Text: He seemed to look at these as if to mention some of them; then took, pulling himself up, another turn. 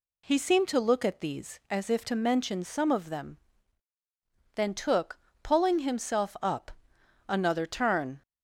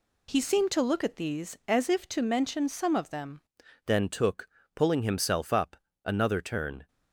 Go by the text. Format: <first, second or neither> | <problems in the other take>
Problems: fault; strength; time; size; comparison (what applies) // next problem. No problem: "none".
first | changes voice at "then"; from 3.8 s on; 3.0 s long